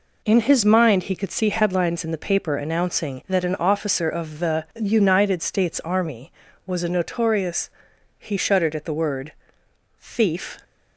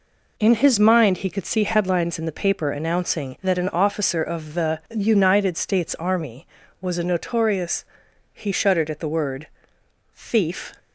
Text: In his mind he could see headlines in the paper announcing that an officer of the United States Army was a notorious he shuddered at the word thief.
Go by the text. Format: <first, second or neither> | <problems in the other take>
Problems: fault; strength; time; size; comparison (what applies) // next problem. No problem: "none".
neither | pauses between "notorious" and "he"; noticeable; the same in both // pauses between "word" and "thief"; noticeable; the same in both